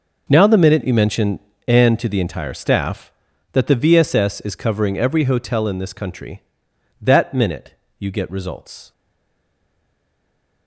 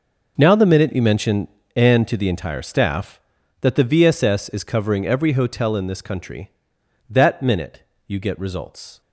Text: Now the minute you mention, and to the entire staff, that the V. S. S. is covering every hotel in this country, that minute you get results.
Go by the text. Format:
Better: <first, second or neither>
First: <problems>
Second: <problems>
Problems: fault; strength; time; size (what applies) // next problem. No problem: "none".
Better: second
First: starts louder than the rest; noticeable; until 1.3 s; 6 dB // pauses between "minute" and "you"; slight; at 7.7 s; 0.24 s long // stays silent after the last word; noticeable; from 8.9 s on; 1.7 s long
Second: starts louder than the rest; noticeable; until 1.3 s; 6 dB // pauses between "minute" and "you"; slight; at 7.8 s; 0.24 s long